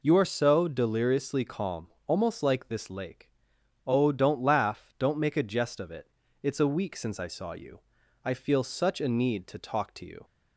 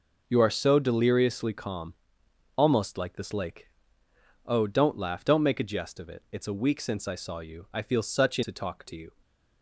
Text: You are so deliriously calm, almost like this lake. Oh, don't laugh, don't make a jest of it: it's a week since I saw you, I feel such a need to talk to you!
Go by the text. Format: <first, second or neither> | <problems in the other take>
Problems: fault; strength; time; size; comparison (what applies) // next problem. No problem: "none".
first | skips "need"; at 8.4 s